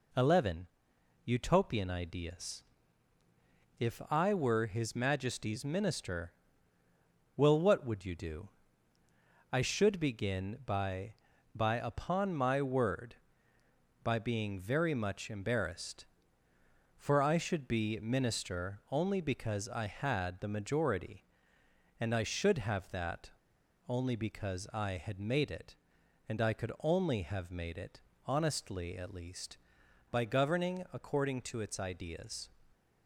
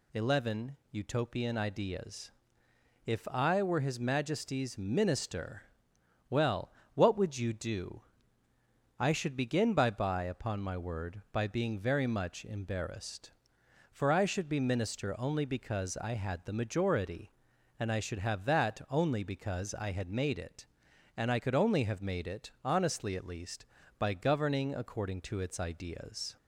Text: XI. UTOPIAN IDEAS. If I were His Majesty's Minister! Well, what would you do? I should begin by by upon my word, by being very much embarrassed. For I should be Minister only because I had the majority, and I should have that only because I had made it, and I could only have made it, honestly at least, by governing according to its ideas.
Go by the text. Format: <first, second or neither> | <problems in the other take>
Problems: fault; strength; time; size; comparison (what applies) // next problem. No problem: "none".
second | pauses between "that" and "only"; noticeable; at 23.3 s; 0.58 s long